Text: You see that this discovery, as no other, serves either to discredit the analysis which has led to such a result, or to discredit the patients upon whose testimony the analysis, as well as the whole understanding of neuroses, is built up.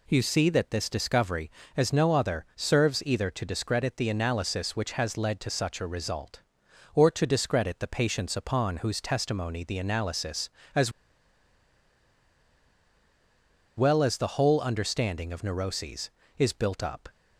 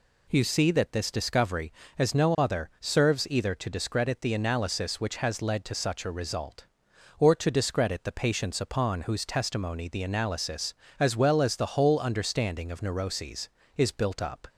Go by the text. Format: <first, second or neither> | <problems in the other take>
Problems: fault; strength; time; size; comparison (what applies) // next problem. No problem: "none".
second | pauses between "as" and "well"; strong; at 10.9 s; 2.8 s long